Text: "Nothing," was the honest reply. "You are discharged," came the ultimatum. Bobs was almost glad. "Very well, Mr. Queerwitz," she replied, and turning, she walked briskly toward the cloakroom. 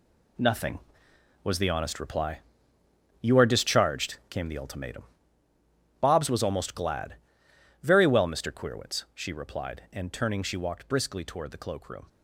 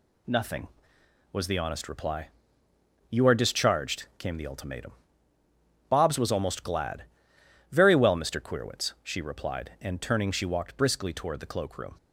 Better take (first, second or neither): second